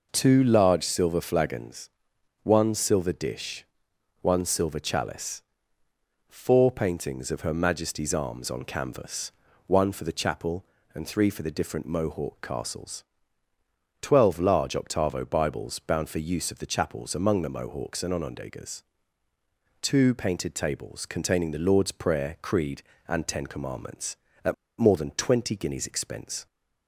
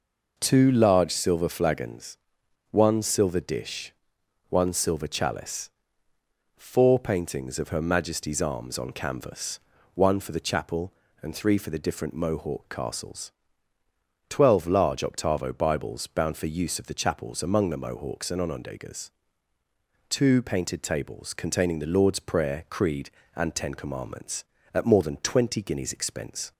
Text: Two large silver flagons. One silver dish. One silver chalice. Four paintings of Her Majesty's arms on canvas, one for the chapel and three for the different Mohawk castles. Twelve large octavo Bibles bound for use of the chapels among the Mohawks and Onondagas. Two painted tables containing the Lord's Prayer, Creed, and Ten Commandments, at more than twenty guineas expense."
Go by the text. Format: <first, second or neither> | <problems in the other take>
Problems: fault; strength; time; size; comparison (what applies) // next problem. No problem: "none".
second | pauses between "at" and "more"; slight; at 24.5 s; 0.25 s long